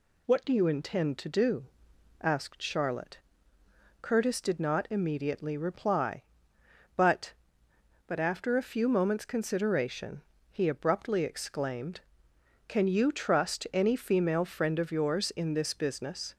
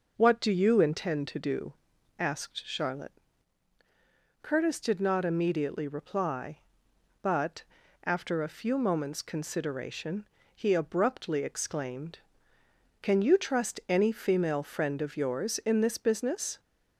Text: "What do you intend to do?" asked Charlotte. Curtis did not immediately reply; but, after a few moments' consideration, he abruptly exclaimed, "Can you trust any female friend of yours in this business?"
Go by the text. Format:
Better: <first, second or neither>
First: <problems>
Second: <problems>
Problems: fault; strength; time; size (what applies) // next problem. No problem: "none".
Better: second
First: says "but" twice; at 8.0 s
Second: none